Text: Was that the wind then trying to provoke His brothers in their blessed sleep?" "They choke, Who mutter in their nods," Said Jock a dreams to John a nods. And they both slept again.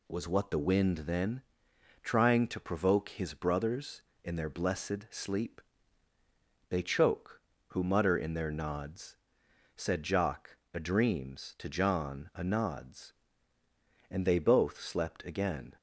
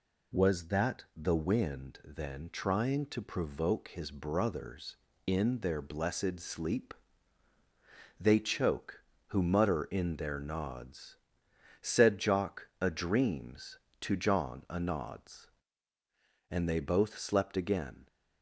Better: second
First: says "what" for "that"; at 0.2 s // pauses between "then" and "trying"; noticeable; at 1.4 s; 0.62 s long // pauses between "Jock" and "a"; slight; at 10.5 s; 0.16 s long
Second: none

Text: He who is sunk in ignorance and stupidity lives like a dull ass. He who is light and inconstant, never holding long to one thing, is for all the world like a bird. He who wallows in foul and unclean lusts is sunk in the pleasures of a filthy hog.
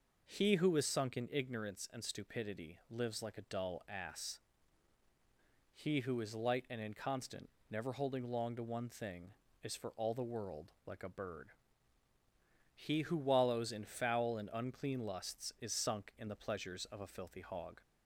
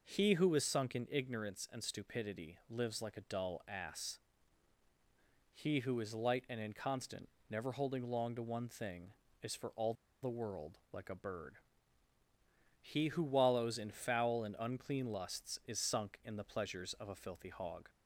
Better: first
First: pauses between "world" and "like"; slight; at 10.7 s; 0.16 s long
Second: pauses between "all" and "the"; slight; at 9.9 s; 0.28 s long // pauses between "world" and "like"; slight; at 10.7 s; 0.16 s long

